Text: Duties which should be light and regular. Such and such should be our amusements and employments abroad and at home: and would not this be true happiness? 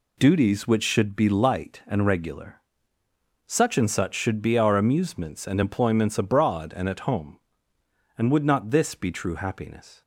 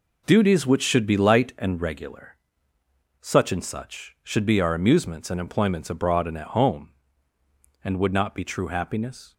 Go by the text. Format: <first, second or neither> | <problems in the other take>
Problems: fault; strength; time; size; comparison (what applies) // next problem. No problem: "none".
first | skips "this"; at 8.3 s